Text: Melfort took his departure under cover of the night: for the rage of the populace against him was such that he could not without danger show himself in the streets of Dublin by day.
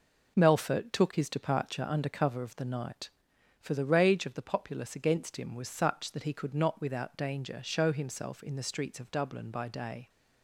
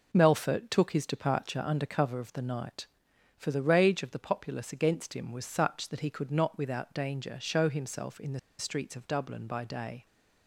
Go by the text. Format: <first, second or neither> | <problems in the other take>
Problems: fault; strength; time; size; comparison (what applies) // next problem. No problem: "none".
first | pauses between "the" and "streets"; slight; at 8.3 s; 0.19 s long